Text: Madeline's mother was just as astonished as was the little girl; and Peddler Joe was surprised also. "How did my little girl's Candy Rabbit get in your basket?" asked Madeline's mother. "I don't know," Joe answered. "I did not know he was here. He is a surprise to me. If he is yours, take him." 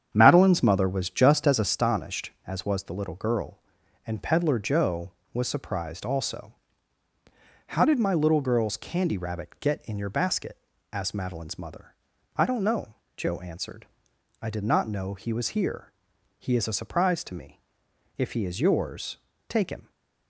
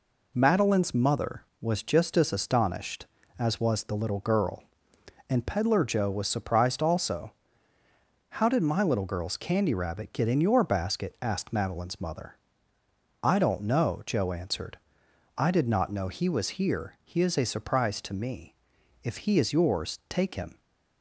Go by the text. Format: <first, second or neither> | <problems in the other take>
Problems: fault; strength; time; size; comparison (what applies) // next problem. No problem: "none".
second | starts louder than the rest; strong; until 1.8 s; 8.5 dB